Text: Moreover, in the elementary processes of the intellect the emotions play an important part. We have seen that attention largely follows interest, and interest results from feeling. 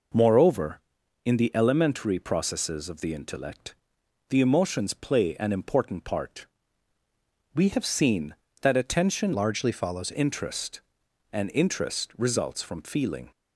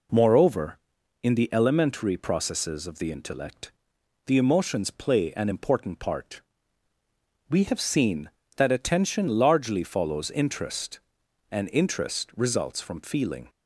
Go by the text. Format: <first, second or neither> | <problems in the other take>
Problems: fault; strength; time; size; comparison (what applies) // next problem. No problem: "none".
second | pauses between "intellect" and "the"; noticeable; at 3.7 s; 0.54 s long; noticeable in the second // changes voice from "largely" to "follows"; from 9.3 to 10.1 s; 0.8 s long